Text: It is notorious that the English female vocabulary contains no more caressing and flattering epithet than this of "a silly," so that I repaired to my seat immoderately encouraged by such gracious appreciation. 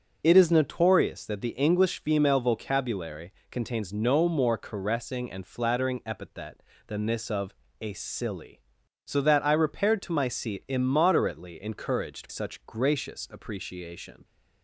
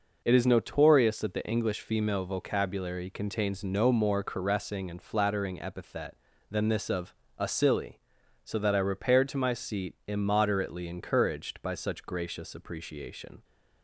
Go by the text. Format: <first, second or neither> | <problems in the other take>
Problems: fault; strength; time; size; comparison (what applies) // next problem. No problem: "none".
second | starts louder than the rest; until 1.2 s; 6 dB // pauses between "vocabulary" and "contains"; slight; at 3.3 s; 0.20 s long // pauses between "of" and "a"; slight; at 7.5 s; 0.26 s long; slight in the second // skips "by"; at 12.2 s